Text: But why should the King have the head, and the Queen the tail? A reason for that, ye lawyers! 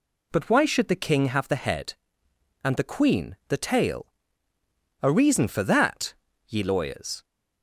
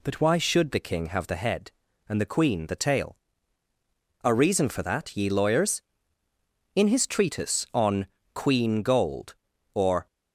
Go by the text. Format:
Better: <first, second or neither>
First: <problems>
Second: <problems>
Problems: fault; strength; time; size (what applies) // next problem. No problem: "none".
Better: first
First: none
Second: goes on to say "In his treatise on Queen Gold or"; strong; from 6.7 s on; 3.3 s long